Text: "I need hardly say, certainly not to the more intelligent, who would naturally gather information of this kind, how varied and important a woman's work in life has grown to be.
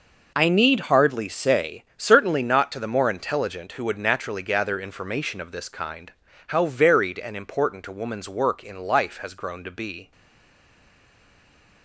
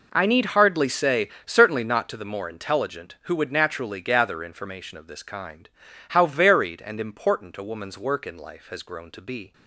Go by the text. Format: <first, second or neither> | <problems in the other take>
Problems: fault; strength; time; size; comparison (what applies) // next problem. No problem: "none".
second | stays silent after the last word; noticeable; from 10.1 s on; 1.7 s long